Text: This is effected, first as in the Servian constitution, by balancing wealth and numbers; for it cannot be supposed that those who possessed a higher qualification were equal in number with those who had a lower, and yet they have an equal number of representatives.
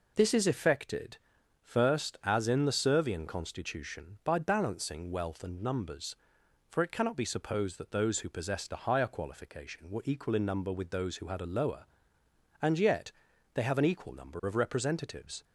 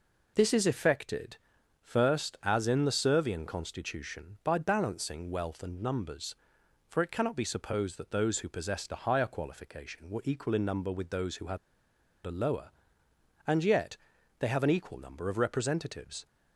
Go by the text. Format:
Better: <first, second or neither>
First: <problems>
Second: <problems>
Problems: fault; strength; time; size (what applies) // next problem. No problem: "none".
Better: first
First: pauses between "yet" and "they"; at 13.1 s; 0.42 s long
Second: pauses between "had" and "a"; noticeable; at 11.5 s; 0.67 s long // pauses between "yet" and "they"; at 13.9 s; 0.42 s long